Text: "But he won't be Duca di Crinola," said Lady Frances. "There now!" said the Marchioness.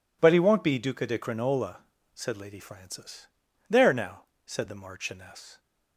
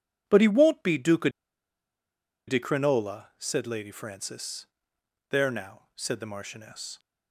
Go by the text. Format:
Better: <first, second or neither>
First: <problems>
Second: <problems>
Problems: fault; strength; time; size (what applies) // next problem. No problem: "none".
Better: first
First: none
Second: pauses between "Duca" and "di"; at 1.2 s; 1.1 s long